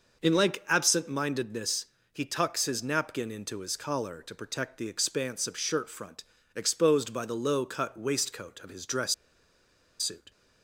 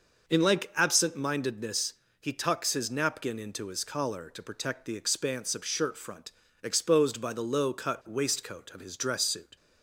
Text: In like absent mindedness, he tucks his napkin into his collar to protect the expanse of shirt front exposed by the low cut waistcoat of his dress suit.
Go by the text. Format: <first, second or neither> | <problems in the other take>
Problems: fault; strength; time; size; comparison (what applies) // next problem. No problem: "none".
second | pauses between "front" and "exposed"; slight; at 6.2 s; 0.32 s long; slight in the second // pauses between "dress" and "suit"; noticeable; at 9.1 s; 0.87 s long